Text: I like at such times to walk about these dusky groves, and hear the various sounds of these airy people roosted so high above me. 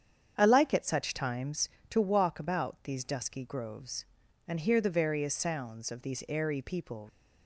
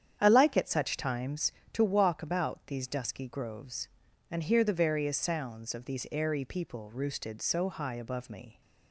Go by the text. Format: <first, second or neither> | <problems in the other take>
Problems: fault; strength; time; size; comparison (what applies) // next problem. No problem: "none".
second | starts louder than the rest; strong; until 1.3 s; 8 dB; strong in the second // stops before "roosted so high above me"; at 7.0 s